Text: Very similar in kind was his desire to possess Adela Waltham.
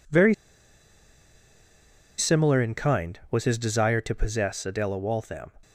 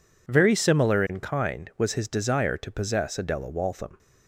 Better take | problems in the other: second | pauses between "Very" and "similar"; strong; at 0.3 s; 1.8 s long

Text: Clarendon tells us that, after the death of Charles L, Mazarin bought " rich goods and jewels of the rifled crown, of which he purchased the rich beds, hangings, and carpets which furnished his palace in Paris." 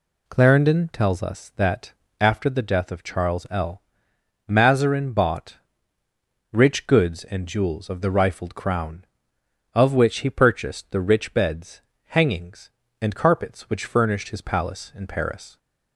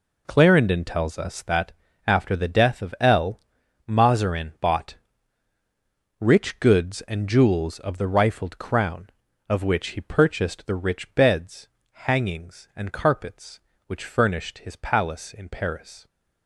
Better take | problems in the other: first | skips "Charles"; at 2.9 s

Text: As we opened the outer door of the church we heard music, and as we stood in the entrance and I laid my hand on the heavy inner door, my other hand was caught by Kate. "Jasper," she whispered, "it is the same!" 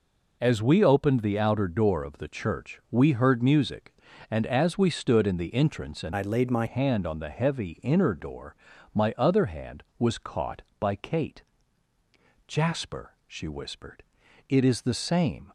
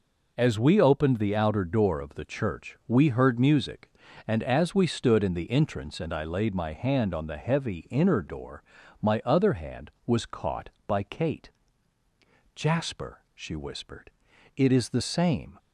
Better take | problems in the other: second | changes voice from "I" to "my"; from 6.1 to 6.6 s; 0.5 s long

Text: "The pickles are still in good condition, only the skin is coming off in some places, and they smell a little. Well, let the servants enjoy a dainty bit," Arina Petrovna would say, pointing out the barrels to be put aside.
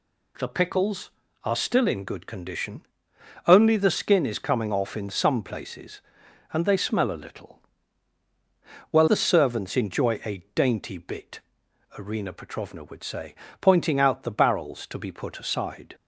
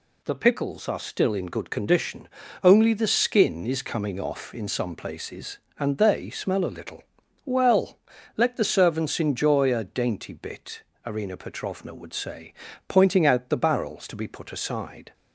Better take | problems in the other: second | skips "let"; at 9.0 s

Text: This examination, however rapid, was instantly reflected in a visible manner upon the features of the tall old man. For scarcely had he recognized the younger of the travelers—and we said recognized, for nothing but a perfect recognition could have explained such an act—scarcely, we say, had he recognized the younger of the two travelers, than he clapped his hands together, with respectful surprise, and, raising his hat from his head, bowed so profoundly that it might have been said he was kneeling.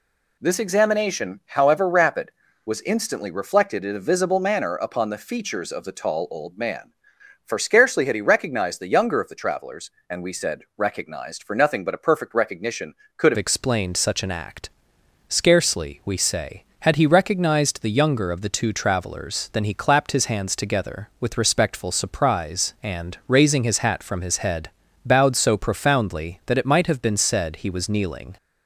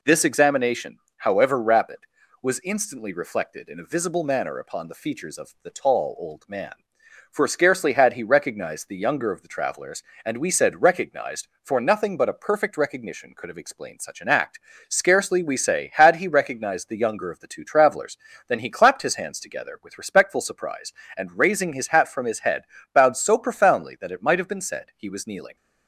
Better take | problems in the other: second | changes voice at "explained"; from 13.3 s on; 15.0 s long

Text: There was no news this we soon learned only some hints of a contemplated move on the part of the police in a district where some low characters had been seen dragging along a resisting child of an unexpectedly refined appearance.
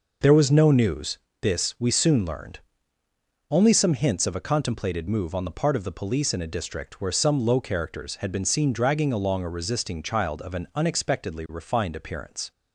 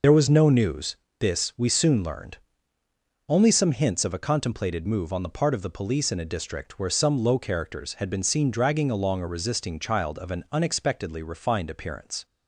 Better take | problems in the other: first | loses the start of "There"; at 0.0 s; 40 ms // pauses between "news" and "this"; slight; at 0.9 s; 0.22 s long; slight in the first // pauses between "learned" and "only"; noticeable; at 2.3 s; 0.90 s long; noticeable in the first

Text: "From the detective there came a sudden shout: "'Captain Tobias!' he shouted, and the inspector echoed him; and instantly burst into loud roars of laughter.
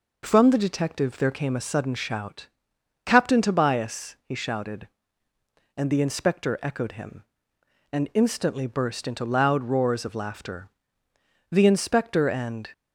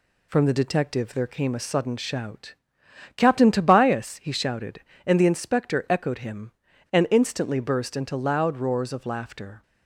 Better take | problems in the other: second | goes on to say "The inspector and"; noticeable; from 11.5 s on; 1.1 s long

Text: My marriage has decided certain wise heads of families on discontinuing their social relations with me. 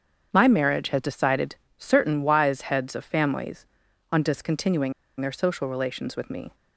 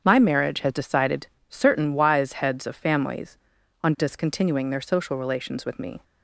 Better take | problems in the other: second | starts louder than the rest; strong; until 1.3 s; 7.5 dB; strong in the second // pauses between "decided" and "certain"; slight; at 1.5 s; 0.24 s long; slight in the second // pauses between "discontinuing" and "their"; slight; at 4.9 s; 0.27 s long

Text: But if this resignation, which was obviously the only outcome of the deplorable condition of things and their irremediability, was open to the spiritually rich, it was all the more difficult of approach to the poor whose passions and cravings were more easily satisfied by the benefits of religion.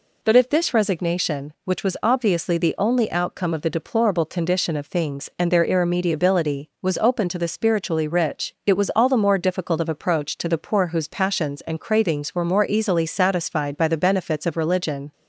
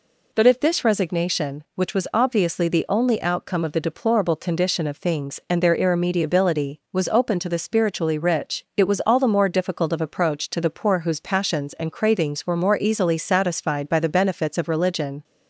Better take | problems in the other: neither | none

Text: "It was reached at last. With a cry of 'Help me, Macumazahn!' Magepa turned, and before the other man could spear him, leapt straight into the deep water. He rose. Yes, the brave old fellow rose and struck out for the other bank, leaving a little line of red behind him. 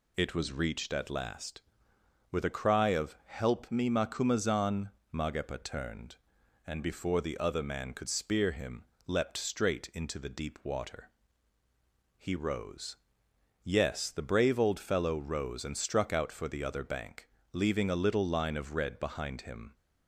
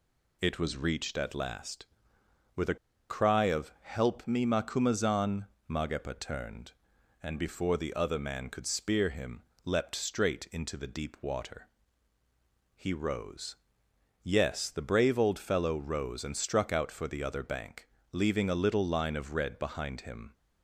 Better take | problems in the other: first | pauses between "a" and "cry"; slight; at 2.7 s; 0.34 s long

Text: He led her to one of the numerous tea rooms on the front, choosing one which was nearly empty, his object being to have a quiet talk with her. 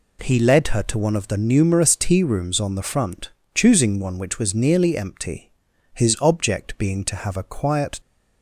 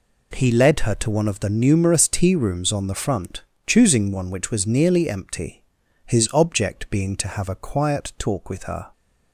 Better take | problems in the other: second | stops before "talk with her"; at 7.9 s

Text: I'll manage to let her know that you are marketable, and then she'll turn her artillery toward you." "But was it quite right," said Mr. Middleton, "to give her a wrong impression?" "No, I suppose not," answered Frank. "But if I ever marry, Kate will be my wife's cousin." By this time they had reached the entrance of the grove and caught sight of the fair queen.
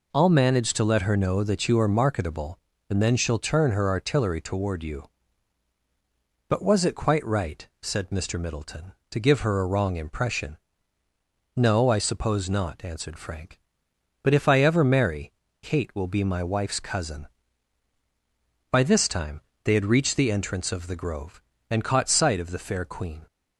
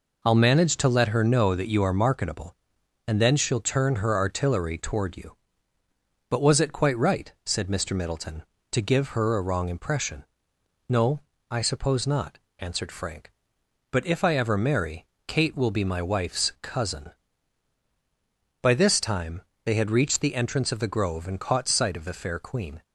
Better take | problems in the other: neither | pauses between "time" and "they"; slight; the same in both

